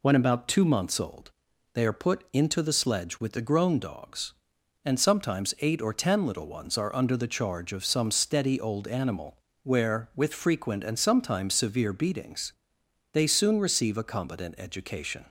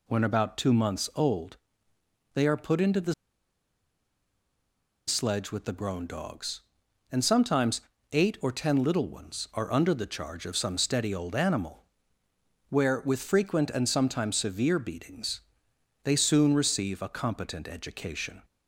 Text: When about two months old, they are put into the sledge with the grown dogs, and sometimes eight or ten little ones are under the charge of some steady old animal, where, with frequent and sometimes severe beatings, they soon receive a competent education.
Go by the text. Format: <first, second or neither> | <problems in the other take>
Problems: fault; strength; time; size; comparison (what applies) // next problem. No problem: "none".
first | pauses between "the" and "sledge"; strong; at 3.1 s; 1.9 s long // pauses between "sometimes" and "eight"; slight; at 7.8 s; 0.32 s long